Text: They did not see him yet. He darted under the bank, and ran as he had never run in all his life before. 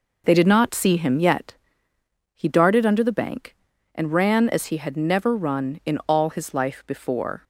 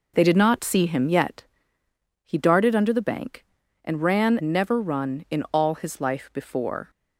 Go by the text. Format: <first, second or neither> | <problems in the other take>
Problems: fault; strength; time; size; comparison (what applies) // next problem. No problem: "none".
first | skips "as he had"; at 4.4 s